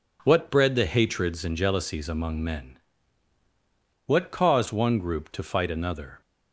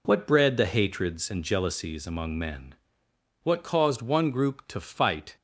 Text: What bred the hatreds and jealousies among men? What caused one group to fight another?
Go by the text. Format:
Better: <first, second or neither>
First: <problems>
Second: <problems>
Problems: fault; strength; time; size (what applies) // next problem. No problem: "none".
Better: first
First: none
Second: stops before "another"; at 5.3 s